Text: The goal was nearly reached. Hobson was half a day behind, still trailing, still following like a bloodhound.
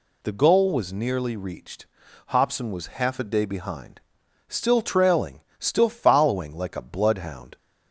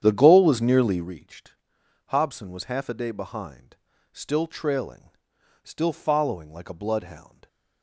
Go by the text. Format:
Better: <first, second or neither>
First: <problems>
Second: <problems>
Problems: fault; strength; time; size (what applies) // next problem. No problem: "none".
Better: first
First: none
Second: starts louder than the rest; strong; until 1.1 s; 9.5 dB